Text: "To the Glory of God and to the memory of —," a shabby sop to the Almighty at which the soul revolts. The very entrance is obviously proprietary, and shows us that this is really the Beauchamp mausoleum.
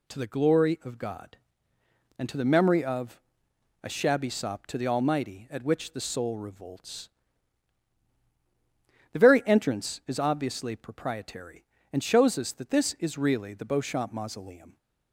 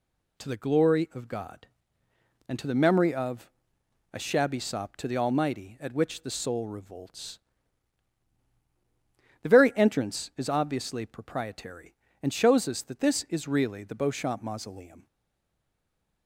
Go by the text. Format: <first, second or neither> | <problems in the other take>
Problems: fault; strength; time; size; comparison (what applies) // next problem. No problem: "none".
first | stays silent after the last word; noticeable; from 15.0 s on; 1.2 s long